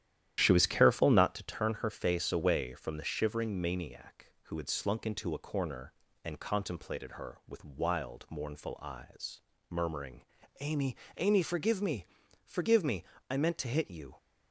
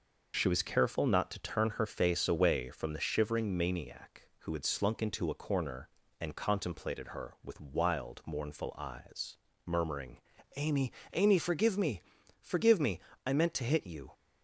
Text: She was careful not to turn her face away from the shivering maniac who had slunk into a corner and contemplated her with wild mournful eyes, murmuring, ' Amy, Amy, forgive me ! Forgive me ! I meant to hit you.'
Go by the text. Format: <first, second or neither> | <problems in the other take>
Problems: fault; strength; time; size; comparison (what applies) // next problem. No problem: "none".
second | starts louder than the rest; strong; until 1.4 s; 11.5 dB